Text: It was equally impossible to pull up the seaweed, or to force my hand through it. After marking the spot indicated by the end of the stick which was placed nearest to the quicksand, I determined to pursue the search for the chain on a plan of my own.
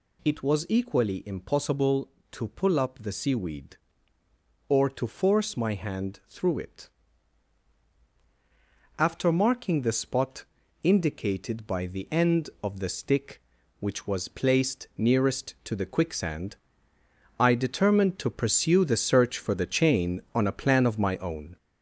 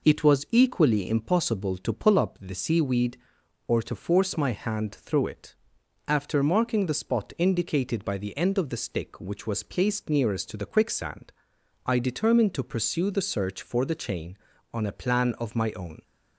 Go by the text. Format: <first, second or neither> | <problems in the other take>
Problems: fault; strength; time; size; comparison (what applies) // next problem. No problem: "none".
second | gets louder; noticeable; throughout; 4.5 dB // pauses between "spot" and "indicated"; at 10.4 s; 0.38 s long